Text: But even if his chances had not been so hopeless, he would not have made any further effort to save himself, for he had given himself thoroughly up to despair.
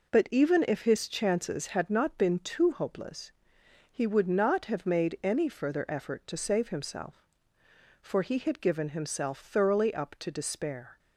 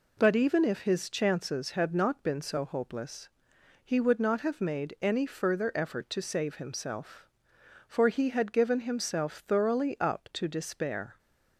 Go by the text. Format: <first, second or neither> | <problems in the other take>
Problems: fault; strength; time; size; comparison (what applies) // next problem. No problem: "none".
second | says "too" for "so"; at 2.3 s